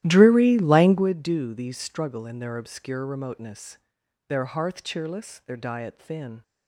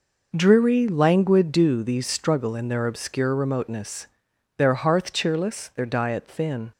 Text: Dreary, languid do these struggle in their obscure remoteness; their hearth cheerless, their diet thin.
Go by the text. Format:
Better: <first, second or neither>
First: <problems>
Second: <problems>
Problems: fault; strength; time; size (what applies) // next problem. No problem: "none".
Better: second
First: starts louder than the rest; strong; until 1.1 s; 14 dB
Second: none